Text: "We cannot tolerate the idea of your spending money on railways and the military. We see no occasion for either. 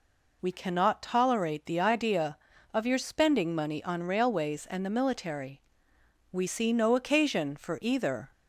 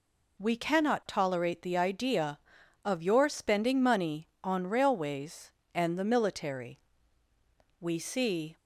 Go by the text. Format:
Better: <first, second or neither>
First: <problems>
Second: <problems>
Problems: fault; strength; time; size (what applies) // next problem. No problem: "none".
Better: first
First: none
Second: stops before "no occasion for either"; at 8.5 s